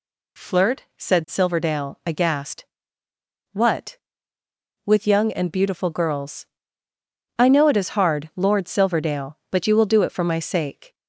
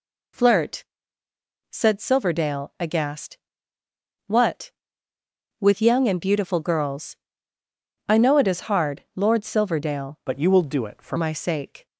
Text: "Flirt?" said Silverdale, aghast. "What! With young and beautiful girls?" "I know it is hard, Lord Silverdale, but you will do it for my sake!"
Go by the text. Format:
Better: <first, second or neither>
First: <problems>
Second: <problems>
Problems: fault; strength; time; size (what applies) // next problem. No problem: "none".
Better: first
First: none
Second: changes voice from "but" to "for"; from 10.2 to 11.1 s; 0.9 s long